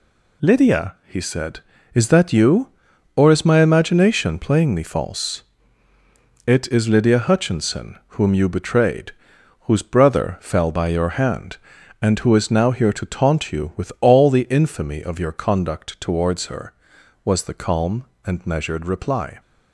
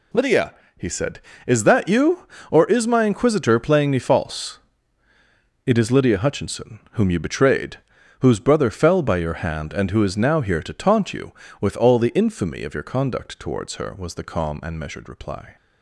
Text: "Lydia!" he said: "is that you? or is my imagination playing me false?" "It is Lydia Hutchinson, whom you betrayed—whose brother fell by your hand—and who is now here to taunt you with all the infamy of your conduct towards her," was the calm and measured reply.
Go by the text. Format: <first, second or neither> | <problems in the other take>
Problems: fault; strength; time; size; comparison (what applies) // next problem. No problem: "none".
first | says "inquisitor" for "imagination"; at 3.0 s